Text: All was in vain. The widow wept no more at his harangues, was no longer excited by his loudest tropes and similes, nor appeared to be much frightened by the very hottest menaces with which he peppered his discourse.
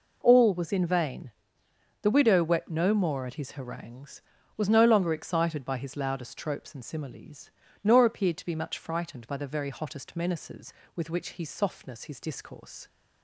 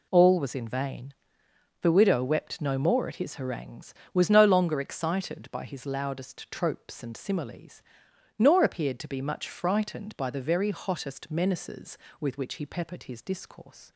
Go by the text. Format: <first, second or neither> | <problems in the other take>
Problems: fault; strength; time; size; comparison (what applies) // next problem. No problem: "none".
second | says "softness" for "peppered"; at 11.4 s